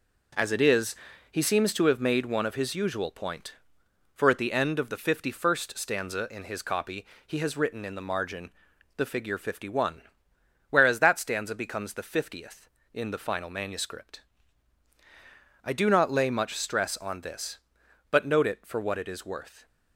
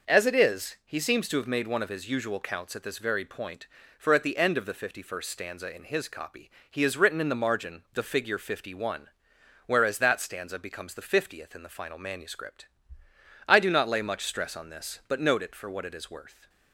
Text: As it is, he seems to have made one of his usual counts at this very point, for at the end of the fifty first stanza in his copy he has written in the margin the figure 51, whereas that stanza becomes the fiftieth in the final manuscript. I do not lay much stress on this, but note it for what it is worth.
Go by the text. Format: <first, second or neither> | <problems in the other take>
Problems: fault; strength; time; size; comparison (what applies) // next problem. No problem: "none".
second | skips "counts at this very"; at 3.1 s // pauses between "copy" and "he"; slight; at 7.0 s; 0.20 s long; slight in the second // pauses between "margin" and "the"; at 8.5 s; 0.44 s long